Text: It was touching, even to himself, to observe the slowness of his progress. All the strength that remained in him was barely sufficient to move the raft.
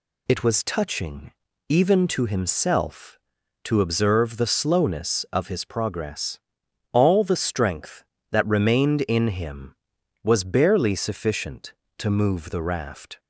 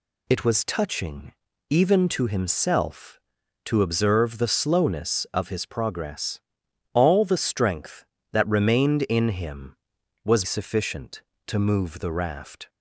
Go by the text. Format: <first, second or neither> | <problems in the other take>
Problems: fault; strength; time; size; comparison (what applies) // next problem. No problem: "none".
first | skips "barely"; at 10.4 s